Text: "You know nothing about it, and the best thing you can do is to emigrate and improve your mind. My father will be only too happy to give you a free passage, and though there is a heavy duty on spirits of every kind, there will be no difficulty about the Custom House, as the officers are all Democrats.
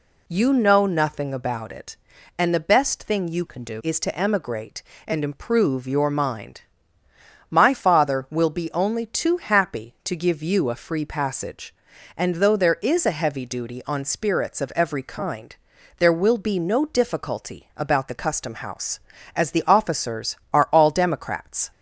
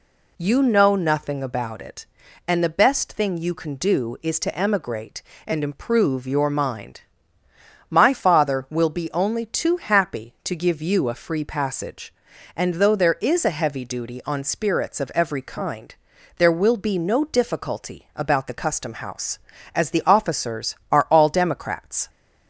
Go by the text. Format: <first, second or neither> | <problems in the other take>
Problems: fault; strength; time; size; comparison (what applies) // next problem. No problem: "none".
second | changes voice from "can" to "do"; from 3.4 to 3.8 s; 0.4 s long